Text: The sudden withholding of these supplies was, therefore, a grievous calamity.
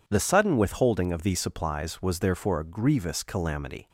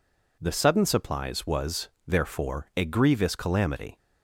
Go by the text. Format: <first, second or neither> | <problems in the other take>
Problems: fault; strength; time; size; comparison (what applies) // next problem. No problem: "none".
first | skips "withholding of these"; at 0.8 s